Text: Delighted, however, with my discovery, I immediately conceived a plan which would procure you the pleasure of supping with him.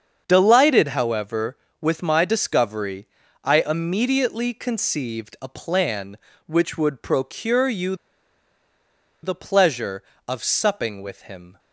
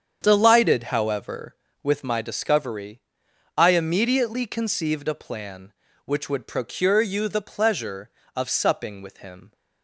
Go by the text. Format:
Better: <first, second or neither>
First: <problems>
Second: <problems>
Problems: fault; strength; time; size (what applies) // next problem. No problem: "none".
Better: second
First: starts louder than the rest; until 1.2 s; 7 dB // pauses between "you" and "the"; strong; at 7.9 s; 1.2 s long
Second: starts louder than the rest; strong; until 1.2 s; 7.5 dB